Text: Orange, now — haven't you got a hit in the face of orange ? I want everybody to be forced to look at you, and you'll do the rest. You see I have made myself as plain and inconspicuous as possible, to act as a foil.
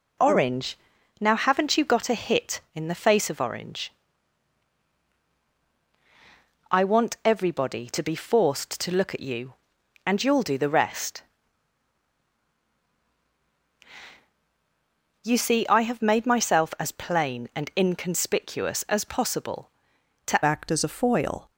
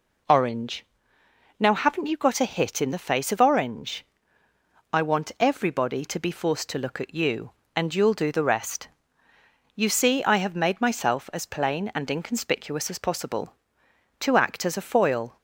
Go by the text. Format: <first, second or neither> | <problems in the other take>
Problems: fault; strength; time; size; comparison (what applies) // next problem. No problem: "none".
second | changes voice at "act"; from 20.4 s on; 1.0 s long